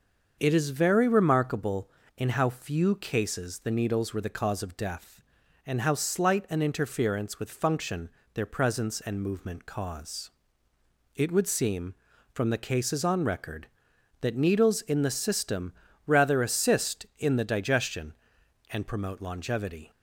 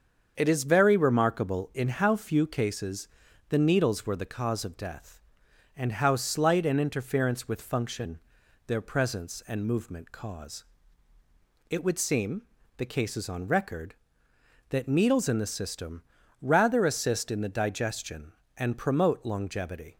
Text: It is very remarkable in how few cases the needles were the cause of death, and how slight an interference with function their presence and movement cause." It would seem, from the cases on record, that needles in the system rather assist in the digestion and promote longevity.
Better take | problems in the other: first | starts louder than the rest; until 1.3 s; 7 dB; also in the first // pauses between "cases" and "the"; at 3.0 s; 0.42 s long // pauses between "function" and "their"; noticeable; at 8.1 s; 0.48 s long; slight in the first // skips "from"; at 12.6 s // pauses between "system" and "rather"; slight; at 16.0 s; 0.36 s long; slight in the first

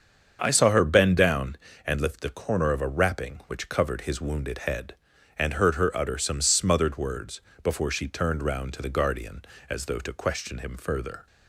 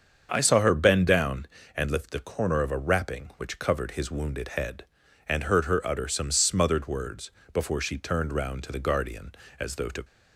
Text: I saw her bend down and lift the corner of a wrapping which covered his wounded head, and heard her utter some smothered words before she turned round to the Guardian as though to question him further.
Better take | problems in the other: first | starts louder than the rest; until 1.3 s; 7 dB; also in the first // pauses between "words" and "before"; slight; at 7.3 s; 0.20 s long; slight in the first // stops before "question him further"; at 10.0 s

